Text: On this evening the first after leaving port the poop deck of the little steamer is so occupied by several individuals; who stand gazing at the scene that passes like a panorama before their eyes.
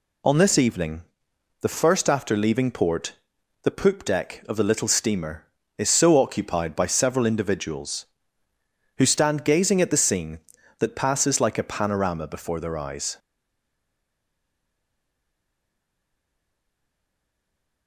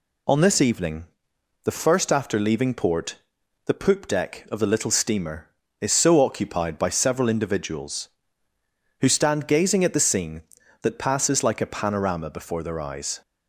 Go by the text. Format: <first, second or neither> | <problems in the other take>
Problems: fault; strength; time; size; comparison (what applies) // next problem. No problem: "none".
second | pauses between "evening" and "the"; noticeable; at 1.0 s; 0.58 s long; noticeable in the second // pauses between "port" and "the"; noticeable; at 3.1 s; 0.50 s long; noticeable in the second // stays silent after the last word; strong; from 13.1 s on; 4.7 s long